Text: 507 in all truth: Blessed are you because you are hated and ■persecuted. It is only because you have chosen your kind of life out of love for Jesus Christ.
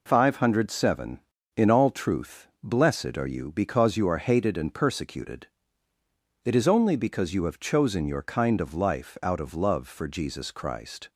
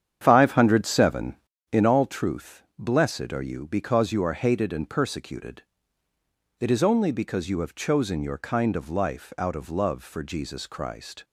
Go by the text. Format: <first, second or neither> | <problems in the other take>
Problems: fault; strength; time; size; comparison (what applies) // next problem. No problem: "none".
first | starts louder than the rest; strong; until 1.8 s; 9 dB